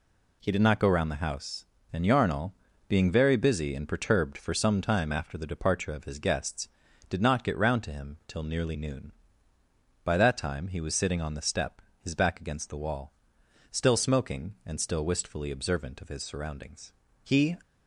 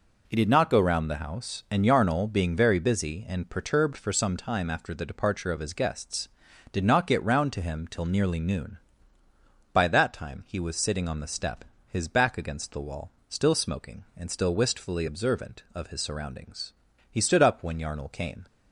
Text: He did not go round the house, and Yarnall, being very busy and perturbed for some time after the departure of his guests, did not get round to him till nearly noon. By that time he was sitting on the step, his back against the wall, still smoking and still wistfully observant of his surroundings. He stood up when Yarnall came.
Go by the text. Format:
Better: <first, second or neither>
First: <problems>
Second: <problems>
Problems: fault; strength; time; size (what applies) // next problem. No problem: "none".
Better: second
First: stops before "stood up when Yarnall came"; at 17.6 s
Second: none